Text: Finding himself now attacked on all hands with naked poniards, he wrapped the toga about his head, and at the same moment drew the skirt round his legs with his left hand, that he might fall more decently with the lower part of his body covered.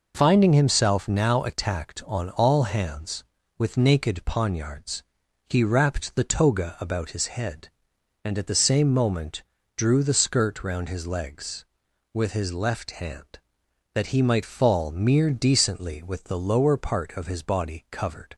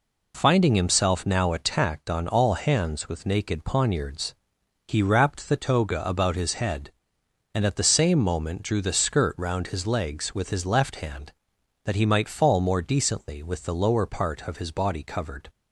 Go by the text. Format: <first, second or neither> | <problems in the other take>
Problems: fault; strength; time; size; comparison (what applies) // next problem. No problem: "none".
second | pauses between "moment" and "drew"; slight; at 9.4 s; 0.34 s long // says "mere" for "more"; at 14.8 s